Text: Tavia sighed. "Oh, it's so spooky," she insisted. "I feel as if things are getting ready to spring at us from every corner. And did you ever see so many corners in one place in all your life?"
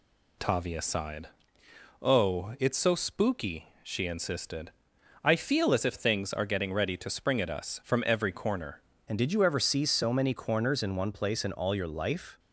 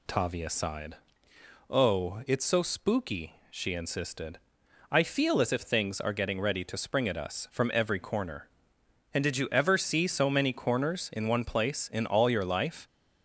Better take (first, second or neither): second